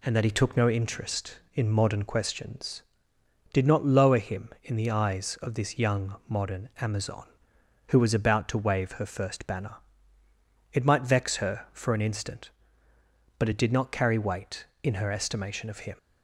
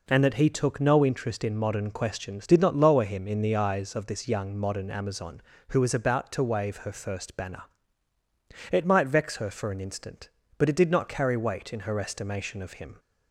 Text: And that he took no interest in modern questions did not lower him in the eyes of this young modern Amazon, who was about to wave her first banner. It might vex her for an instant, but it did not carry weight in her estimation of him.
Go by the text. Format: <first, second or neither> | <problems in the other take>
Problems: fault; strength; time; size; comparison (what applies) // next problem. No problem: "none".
neither | none